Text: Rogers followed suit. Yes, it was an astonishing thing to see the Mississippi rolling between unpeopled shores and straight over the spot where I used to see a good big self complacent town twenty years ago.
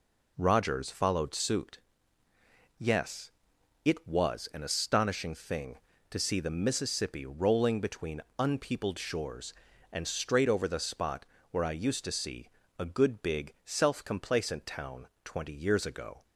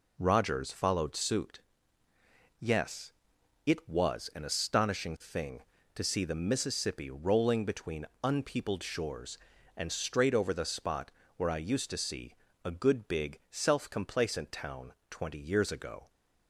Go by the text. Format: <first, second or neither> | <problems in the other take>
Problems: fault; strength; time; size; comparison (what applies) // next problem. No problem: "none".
neither | pauses between "between" and "unpeopled"; slight; the same in both // pauses between "spot" and "where"; slight; the same in both // pauses between "see" and "a"; slight; the same in both // pauses between "town" and "twenty"; slight; the same in both